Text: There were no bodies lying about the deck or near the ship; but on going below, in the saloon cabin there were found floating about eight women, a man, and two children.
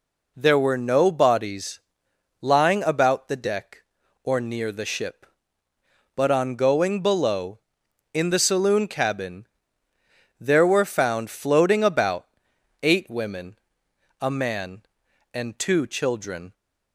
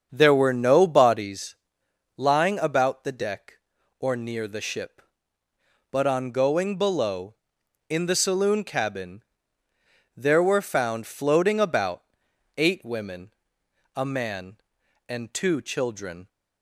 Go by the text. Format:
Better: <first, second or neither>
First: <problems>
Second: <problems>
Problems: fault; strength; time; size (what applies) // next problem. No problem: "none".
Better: first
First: pauses between "bodies" and "lying"; noticeable; at 1.7 s; 0.60 s long // pauses between "cabin" and "there"; noticeable; at 9.4 s; 0.92 s long // pauses between "about" and "eight"; noticeable; at 12.2 s; 0.54 s long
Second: starts louder than the rest; strong; until 1.4 s; 7 dB // pauses between "bodies" and "lying"; noticeable; at 1.5 s; 0.60 s long // pauses between "cabin" and "there"; noticeable; at 9.2 s; 0.92 s long // pauses between "about" and "eight"; noticeable; at 12.0 s; 0.52 s long